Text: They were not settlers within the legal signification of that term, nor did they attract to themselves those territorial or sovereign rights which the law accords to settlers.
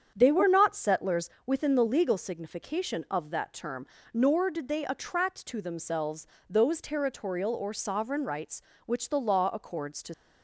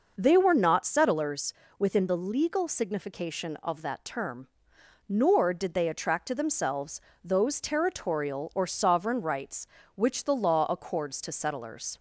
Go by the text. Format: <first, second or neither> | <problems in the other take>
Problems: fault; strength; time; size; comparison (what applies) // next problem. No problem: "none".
second | starts louder than the rest; strong; until 1.1 s; 8 dB // pauses between "settlers" and "within"; slight; at 1.3 s; 0.16 s long; slight in the second // pauses between "themselves" and "those"; slight; at 6.2 s; 0.22 s long; slight in the second // stops before "settlers"; at 10.1 s